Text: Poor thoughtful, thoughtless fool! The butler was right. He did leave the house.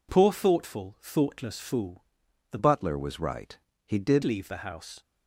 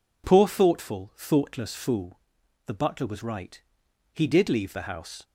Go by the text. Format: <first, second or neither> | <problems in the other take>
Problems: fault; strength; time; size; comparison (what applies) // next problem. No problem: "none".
second | changes voice from "butler" to "did"; from 2.5 to 4.2 s; 1.7 s long